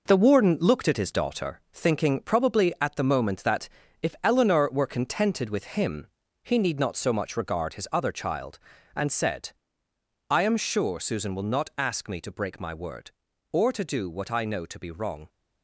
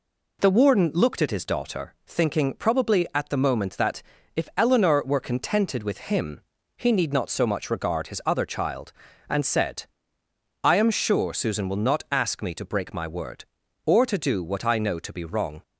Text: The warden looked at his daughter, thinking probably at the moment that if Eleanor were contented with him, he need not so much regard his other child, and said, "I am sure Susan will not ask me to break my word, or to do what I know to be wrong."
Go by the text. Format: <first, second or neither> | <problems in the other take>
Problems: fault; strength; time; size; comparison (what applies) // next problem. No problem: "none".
second | gets quieter; strong; throughout; 8 dB // pauses between "that" and "if"; slight; at 3.6 s; 0.34 s long; slight in the second